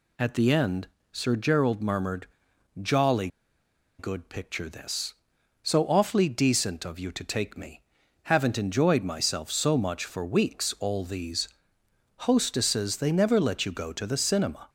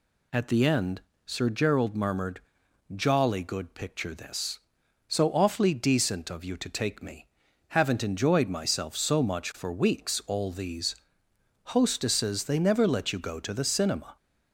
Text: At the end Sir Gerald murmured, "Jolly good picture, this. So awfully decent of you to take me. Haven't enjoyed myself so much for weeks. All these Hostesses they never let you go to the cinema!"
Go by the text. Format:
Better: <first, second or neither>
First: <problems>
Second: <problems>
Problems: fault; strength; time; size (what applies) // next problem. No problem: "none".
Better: second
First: pauses between "end" and "Sir"; slight; at 0.8 s; 0.24 s long // pauses between "Jolly" and "good"; noticeable; at 3.2 s; 0.70 s long // pauses between "these" and "Hostesses"; noticeable; at 11.4 s; 0.70 s long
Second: pauses between "end" and "Sir"; slight; at 0.9 s; 0.24 s long // pauses between "these" and "Hostesses"; noticeable; at 10.9 s; 0.70 s long